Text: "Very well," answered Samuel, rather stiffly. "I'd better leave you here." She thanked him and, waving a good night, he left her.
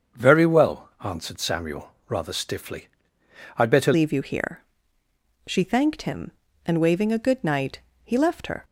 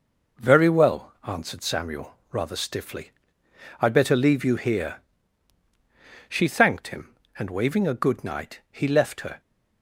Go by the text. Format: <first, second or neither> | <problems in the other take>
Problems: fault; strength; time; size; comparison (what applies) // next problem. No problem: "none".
second | starts louder than the rest; until 1.3 s; 7 dB // changes voice at "leave"; from 3.9 s on; 4.7 s long